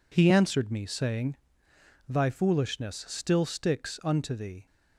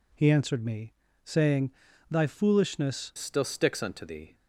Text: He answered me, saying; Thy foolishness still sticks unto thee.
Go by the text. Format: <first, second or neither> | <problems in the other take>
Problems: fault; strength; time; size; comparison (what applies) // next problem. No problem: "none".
first | changes voice at "still"; from 3.1 s on; 1.2 s long